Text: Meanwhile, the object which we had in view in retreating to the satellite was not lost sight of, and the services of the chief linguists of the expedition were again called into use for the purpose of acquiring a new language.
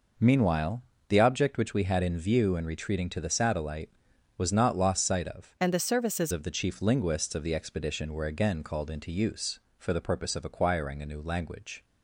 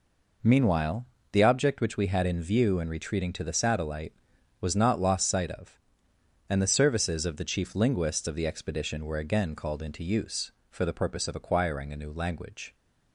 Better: second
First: changes voice from "and" to "services"; from 5.5 to 6.3 s; 0.8 s long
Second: none

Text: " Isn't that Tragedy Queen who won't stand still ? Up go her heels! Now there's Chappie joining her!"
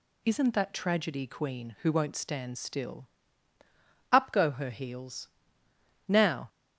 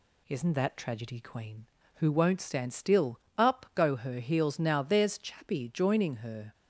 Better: second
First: stops before "there's Chappie joining her"; at 6.4 s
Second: none

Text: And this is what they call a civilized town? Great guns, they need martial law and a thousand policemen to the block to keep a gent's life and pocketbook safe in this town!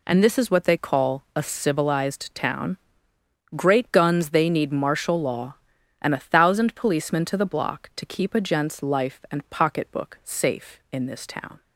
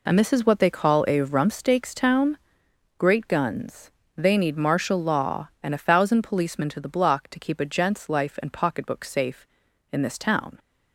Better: first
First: none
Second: says "rumpsteaks" for "civilized"; at 1.1 s

